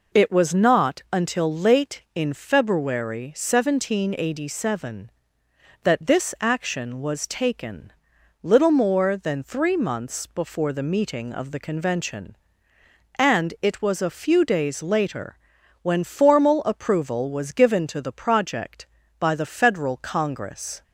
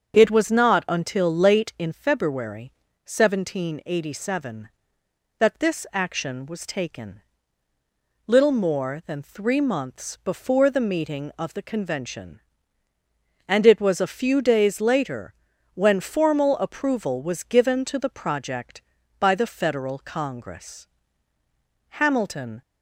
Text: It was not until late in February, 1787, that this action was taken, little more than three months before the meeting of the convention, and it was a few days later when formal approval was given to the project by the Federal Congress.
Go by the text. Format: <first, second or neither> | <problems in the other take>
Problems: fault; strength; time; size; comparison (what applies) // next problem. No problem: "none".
first | starts louder than the rest; until 1.1 s; 7 dB // pauses between "later" and "when"; at 15.3 s; 0.42 s long; noticeable in the first // goes on to say "Hamilton"; noticeable; from 21.9 s on; 0.64 s long